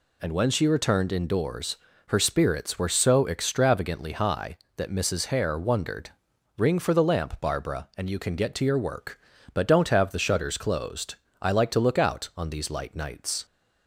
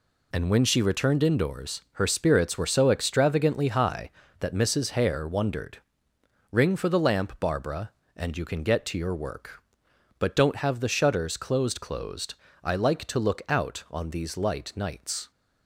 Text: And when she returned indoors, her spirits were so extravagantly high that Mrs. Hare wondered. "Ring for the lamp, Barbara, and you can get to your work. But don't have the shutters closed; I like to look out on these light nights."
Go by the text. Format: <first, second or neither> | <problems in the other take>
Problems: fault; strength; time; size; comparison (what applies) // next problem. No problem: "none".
first | says "closed" twice; at 11.8 s